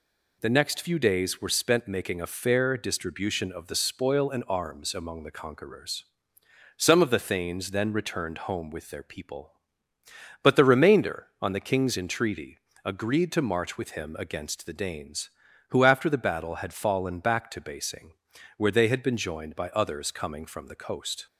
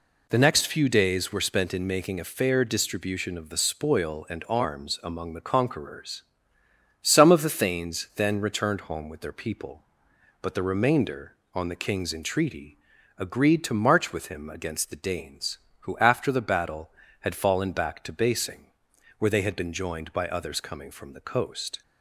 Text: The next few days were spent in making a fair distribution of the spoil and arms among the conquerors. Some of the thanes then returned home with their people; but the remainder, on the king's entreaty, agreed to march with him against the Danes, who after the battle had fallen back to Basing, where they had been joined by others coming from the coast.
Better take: second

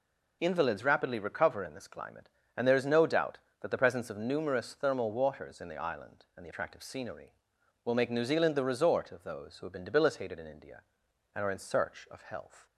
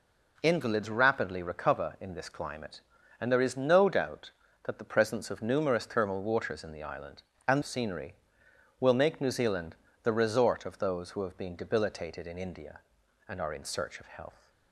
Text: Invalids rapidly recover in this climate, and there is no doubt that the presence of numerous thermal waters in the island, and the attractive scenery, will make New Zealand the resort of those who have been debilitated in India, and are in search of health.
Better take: first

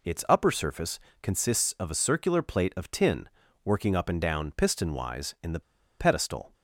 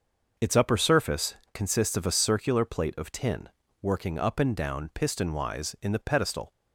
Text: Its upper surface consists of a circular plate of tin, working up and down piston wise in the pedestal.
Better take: second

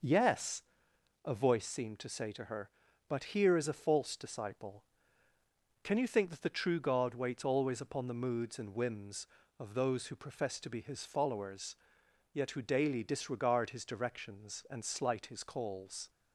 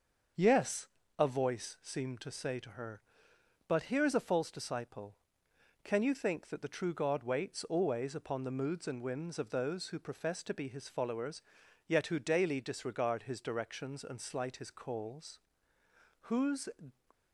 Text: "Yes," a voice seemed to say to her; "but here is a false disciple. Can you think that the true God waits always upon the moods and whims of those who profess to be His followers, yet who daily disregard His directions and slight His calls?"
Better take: first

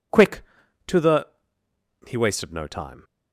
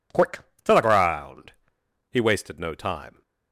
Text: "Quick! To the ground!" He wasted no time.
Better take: second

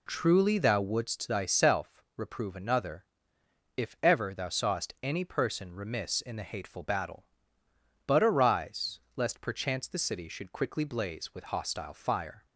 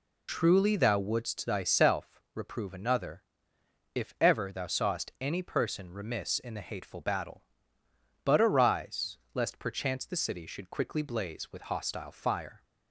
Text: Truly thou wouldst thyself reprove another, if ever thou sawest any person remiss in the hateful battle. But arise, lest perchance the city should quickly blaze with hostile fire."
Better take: first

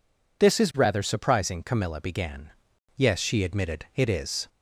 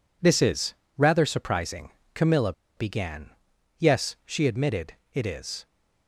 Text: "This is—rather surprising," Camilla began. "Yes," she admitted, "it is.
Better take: first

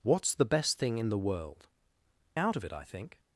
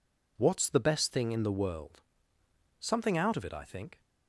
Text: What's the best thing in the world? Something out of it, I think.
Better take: second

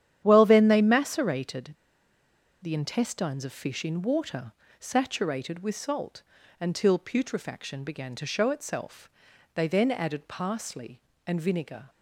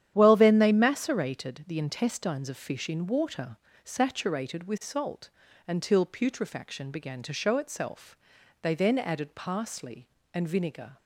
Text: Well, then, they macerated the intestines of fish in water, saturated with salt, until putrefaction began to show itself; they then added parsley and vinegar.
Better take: second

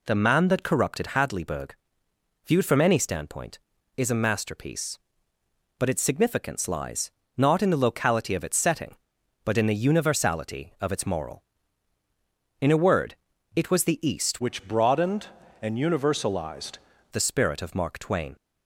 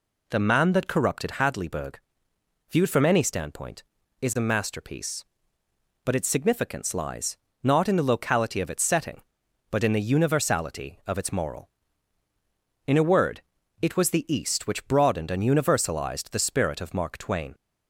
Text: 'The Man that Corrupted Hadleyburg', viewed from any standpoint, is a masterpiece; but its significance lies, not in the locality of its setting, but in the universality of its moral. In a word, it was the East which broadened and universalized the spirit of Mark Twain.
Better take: second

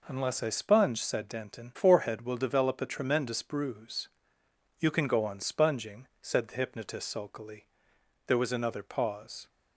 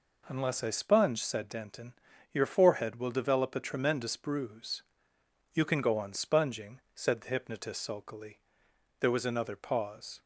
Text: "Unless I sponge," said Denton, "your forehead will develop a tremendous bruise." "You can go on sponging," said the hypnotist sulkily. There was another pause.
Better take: second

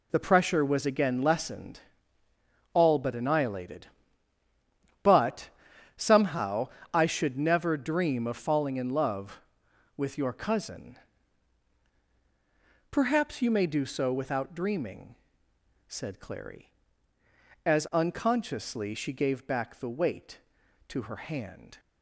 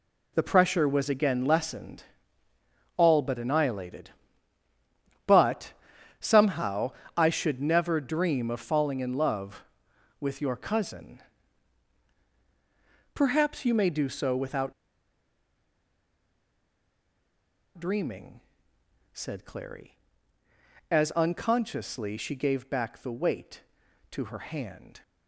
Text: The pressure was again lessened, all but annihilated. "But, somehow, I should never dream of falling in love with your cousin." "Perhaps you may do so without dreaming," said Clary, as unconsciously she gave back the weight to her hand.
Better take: first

